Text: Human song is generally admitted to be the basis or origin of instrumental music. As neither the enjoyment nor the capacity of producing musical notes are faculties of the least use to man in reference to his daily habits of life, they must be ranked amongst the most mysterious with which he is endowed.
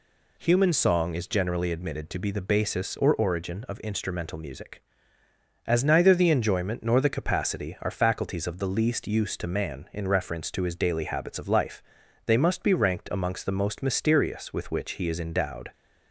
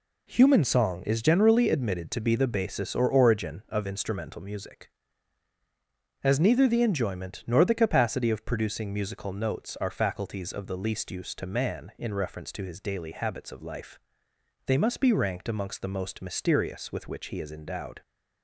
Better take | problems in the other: second | skips "of producing musical notes"; at 7.7 s

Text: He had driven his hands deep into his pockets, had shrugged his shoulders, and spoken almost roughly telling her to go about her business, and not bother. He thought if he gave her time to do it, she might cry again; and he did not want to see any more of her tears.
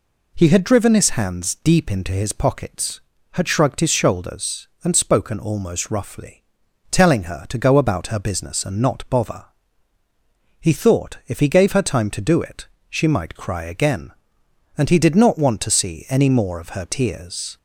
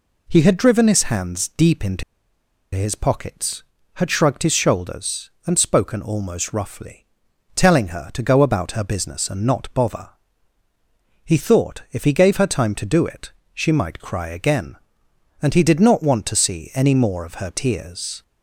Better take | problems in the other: first | pauses between "into" and "his"; noticeable; at 2.0 s; 0.71 s long // pauses between "roughly" and "telling"; noticeable; at 7.0 s; 0.52 s long; noticeable in the first

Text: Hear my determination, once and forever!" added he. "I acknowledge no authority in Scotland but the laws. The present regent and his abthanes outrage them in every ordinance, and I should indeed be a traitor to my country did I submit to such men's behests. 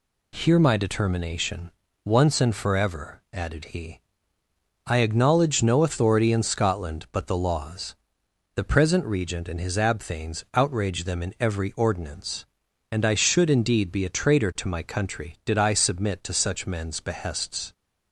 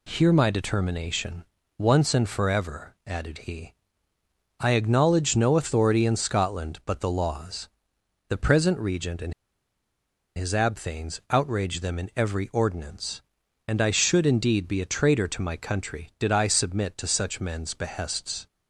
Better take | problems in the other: first | pauses between "and" and "his"; at 9.3 s; 1.0 s long

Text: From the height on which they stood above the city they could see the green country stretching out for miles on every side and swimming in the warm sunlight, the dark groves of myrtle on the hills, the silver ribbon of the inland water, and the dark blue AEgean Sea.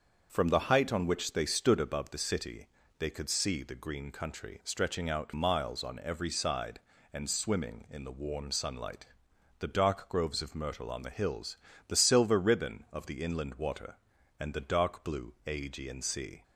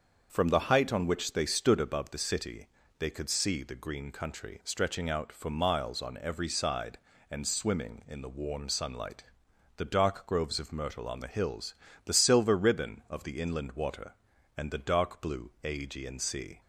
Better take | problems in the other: second | starts louder than the rest; until 1.3 s; 6.5 dB; also in the second // pauses between "city" and "they"; slight; at 2.6 s; 0.32 s long; slight in the second // skips "for"; at 5.3 s

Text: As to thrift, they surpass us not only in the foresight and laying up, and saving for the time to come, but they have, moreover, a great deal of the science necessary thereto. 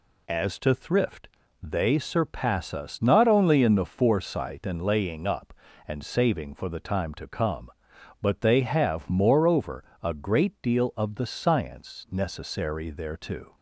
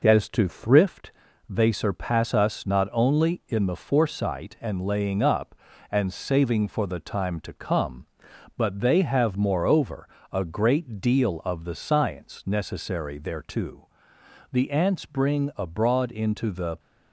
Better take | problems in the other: first | goes on to say "The ants bring abroad into the"; strong; from 14.5 s on; 2.2 s long

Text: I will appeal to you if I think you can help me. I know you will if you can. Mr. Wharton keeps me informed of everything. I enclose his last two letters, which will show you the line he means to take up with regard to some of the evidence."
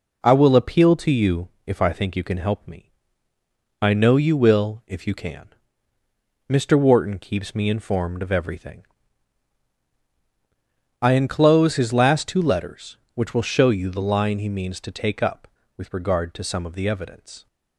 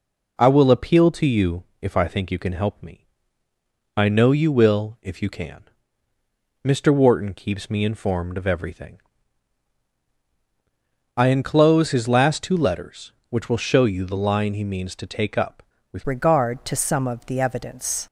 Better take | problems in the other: first | pauses between "you" and "if"; slight; at 1.6 s; 0.18 s long; slight in the first // changes voice at "regard"; from 16.0 s on; 2.0 s long

